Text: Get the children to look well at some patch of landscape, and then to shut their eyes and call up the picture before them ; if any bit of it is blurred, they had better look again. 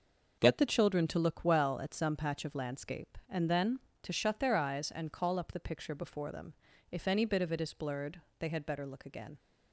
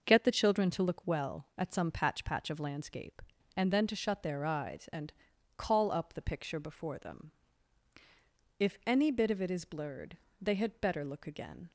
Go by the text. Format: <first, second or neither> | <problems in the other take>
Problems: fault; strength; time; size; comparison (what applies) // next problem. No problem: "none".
first | says "patch" twice; at 2.2 s // pauses between "and" and "call"; at 5.1 s; 0.44 s long